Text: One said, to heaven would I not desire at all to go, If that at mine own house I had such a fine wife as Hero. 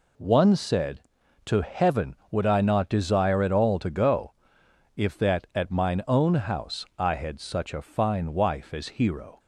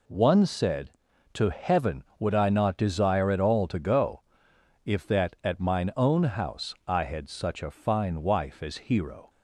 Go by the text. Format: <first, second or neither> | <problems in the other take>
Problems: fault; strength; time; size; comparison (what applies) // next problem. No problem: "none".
neither | none